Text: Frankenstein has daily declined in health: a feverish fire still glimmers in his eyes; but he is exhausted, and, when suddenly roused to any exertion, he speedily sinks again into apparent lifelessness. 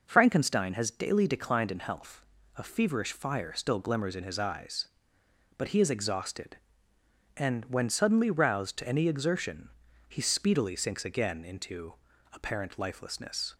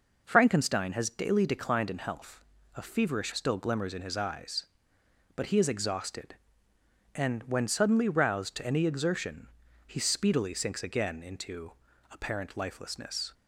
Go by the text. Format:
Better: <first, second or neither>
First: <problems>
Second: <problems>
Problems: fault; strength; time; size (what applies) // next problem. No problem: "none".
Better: first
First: pauses between "into" and "apparent"; at 11.9 s; 0.38 s long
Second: skips "fire"; at 3.3 s // pauses between "into" and "apparent"; at 11.7 s; 0.38 s long